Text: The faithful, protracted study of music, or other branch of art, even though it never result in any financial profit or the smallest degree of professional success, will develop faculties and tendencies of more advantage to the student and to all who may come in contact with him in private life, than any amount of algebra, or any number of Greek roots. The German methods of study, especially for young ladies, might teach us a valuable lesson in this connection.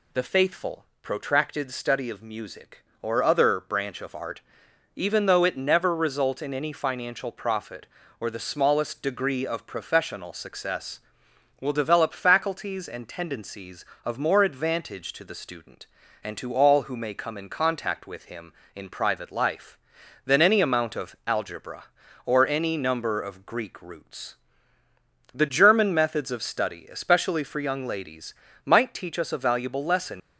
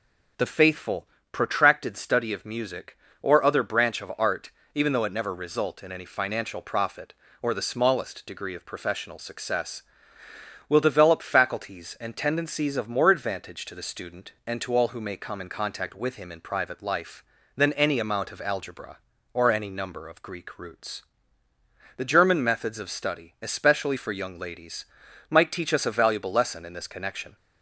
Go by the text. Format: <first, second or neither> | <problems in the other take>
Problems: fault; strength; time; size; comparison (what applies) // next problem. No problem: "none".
second | stops before "in this connection"; at 30.2 s